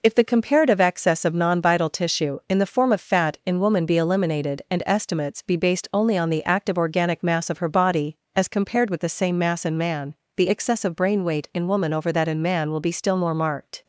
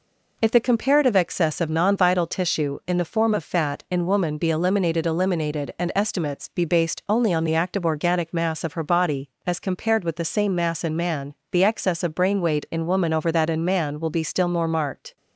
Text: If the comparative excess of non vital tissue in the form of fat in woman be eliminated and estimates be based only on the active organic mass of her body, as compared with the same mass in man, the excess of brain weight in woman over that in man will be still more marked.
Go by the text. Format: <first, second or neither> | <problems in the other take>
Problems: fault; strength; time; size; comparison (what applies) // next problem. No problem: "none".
first | says "eliminated" twice; at 5.0 s